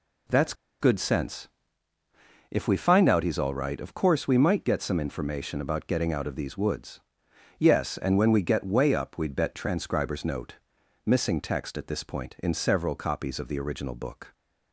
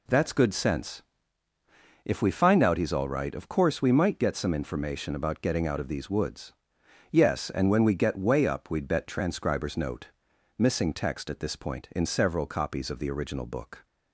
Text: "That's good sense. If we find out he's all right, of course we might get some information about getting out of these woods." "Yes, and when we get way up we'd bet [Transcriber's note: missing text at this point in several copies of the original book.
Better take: second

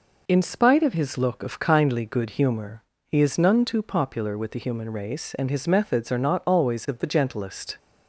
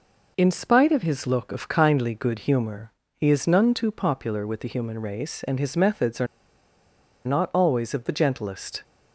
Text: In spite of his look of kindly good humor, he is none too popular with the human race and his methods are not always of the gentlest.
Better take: first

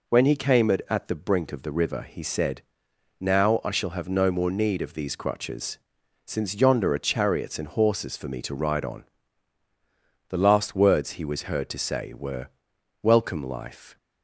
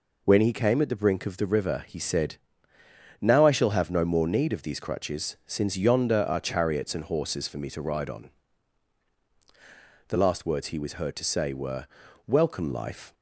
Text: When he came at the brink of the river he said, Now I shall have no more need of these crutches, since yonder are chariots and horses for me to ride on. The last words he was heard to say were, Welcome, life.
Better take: second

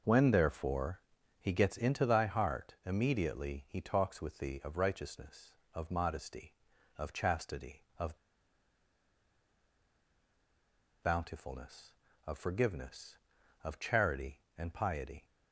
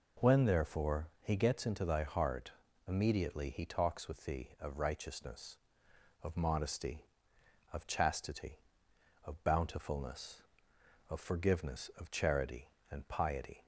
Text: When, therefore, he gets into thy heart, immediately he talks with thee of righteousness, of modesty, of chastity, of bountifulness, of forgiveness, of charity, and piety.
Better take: second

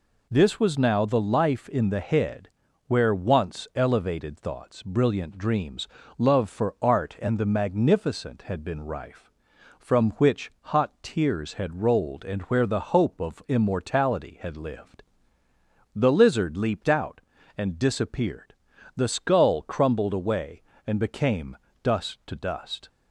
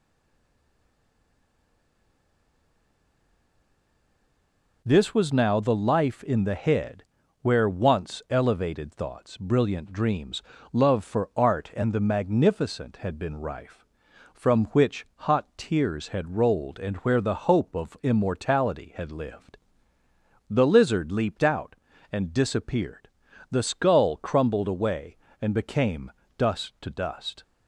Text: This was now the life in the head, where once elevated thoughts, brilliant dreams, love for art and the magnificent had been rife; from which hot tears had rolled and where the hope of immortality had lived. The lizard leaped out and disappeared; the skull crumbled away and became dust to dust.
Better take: first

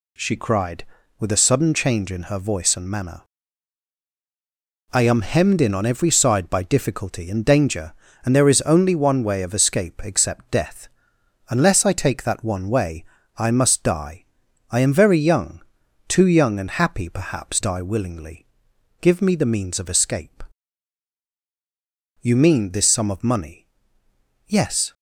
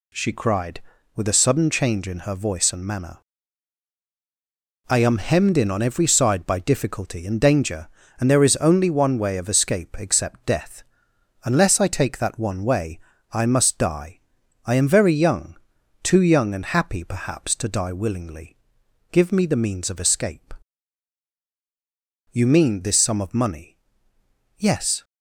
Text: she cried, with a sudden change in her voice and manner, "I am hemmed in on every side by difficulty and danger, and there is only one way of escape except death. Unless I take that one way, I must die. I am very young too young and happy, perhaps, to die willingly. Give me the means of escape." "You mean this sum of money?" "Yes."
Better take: second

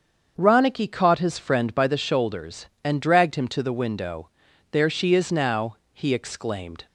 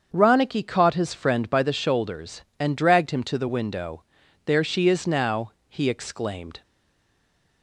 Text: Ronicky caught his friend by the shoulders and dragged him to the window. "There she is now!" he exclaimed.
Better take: first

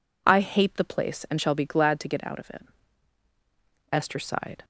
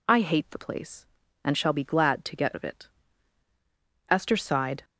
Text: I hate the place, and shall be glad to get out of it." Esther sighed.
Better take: first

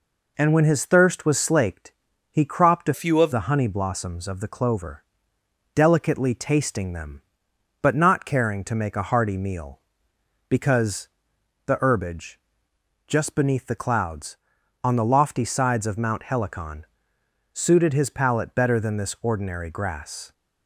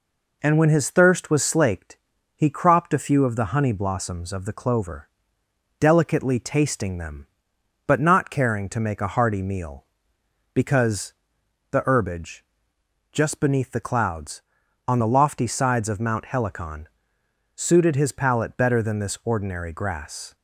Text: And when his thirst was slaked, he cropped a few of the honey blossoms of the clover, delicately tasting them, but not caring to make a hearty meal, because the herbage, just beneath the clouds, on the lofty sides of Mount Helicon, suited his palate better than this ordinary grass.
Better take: second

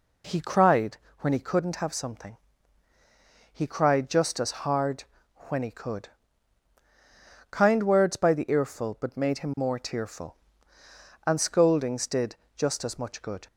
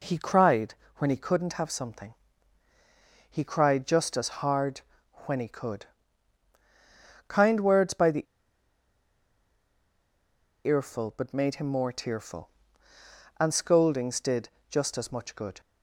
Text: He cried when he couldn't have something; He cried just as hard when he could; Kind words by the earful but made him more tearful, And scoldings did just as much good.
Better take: first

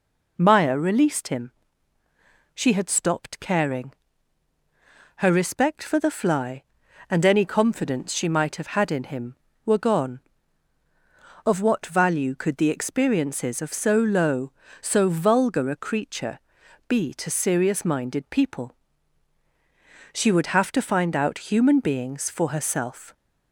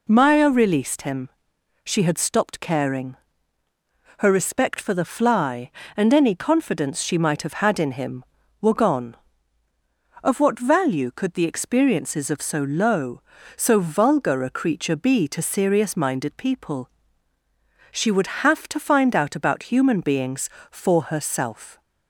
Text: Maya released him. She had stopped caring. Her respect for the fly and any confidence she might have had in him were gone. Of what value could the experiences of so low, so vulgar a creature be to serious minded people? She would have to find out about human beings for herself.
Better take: second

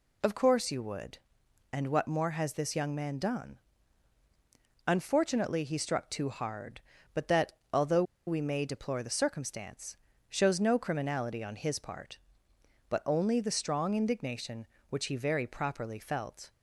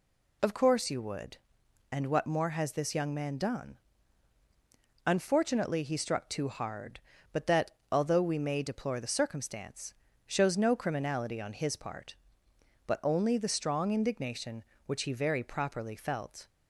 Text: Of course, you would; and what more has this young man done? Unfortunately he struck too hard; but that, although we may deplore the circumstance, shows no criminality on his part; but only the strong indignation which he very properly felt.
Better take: second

